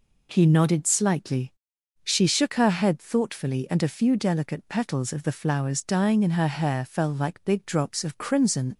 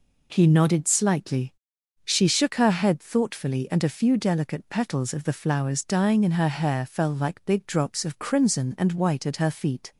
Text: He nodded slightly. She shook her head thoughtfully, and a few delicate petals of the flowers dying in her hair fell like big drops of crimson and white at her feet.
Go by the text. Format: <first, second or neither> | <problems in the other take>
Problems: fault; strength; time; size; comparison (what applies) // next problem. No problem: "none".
second | stops before "and white at her feet"; at 8.7 s